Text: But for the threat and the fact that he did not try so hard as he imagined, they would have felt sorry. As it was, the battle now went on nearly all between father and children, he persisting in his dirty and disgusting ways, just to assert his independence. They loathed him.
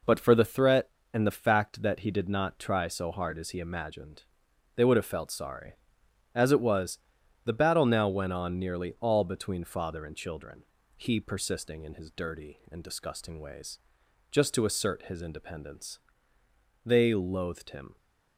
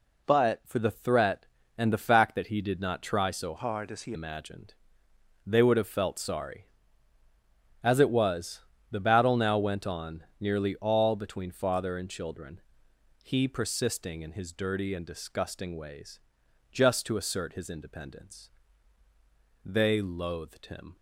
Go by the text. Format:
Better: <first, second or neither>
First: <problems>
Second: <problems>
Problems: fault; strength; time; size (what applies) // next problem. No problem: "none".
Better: first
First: none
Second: changes voice from "hard" to "he"; from 3.5 to 4.1 s; 0.6 s long // pauses between "on" and "nearly"; slight; at 10.2 s; 0.16 s long